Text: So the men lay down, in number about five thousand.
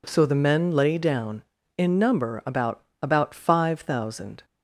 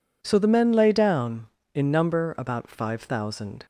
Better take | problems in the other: second | says "about" twice; at 3.0 s

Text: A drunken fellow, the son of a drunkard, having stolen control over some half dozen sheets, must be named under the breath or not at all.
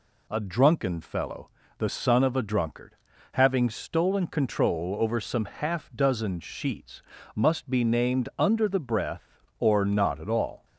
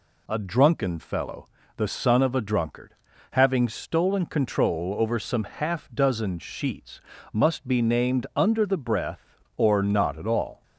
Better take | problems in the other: neither | none

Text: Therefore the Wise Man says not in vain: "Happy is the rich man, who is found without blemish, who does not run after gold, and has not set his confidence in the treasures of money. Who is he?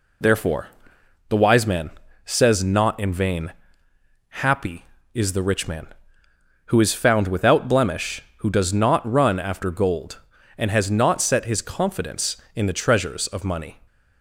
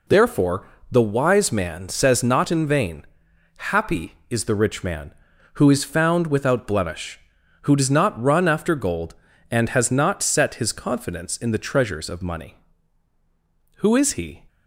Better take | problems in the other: second | pauses between "Therefore" and "the"; noticeable; at 0.6 s; 0.62 s long; slight in the second // pauses between "Man" and "says"; slight; at 1.8 s; 0.34 s long // stops before "Who is he"; at 13.8 s

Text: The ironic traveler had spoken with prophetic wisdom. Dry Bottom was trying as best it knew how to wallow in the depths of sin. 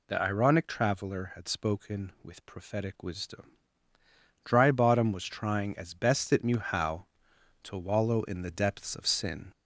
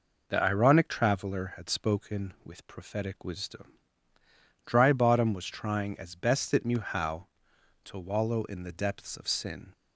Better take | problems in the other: second | gets louder; slight; throughout; 3 dB

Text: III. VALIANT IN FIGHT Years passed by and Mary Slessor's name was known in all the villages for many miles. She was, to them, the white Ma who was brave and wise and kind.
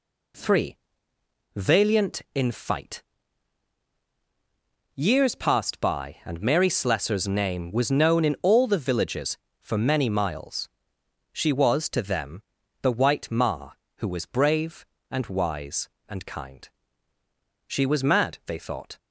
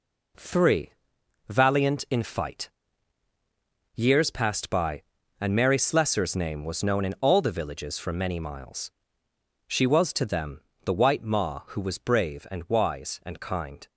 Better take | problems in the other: second | pauses between "FIGHT" and "Years"; strong; at 3.0 s; 1.9 s long; strong in the second // goes on to say "She was mad they thought"; from 17.6 s on; 1.3 s long

